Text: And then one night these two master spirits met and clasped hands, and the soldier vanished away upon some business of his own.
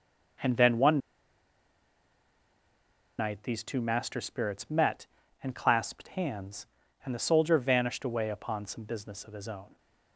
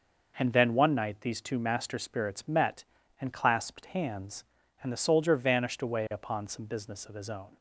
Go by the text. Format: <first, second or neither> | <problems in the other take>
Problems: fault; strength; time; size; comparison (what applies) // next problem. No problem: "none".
second | pauses between "one" and "night"; strong; at 0.9 s; 2.1 s long